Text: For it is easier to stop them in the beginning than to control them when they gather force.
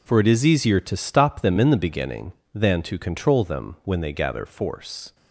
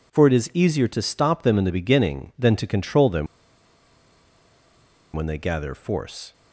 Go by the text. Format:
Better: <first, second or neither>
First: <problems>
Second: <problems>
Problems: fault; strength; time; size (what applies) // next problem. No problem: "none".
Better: first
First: none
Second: pauses between "them" and "when"; strong; at 3.2 s; 1.8 s long